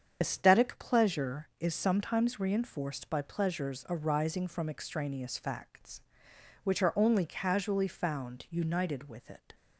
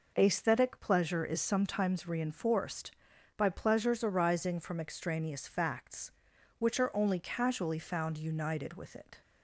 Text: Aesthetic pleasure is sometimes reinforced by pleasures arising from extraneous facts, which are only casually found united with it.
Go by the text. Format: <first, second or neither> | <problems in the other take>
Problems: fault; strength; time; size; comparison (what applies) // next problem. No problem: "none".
second | loses the start of "Aesthetic"; at 0.2 s; 45 ms // starts louder than the rest; strong; until 1.2 s; 7.5 dB